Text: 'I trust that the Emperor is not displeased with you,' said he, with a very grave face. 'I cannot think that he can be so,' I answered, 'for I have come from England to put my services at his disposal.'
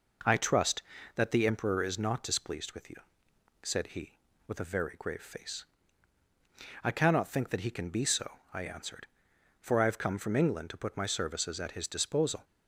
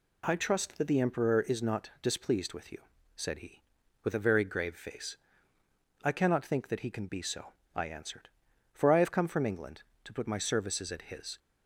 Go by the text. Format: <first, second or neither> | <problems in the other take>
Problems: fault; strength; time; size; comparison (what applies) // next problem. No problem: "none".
first | stops before "disposal"; at 11.3 s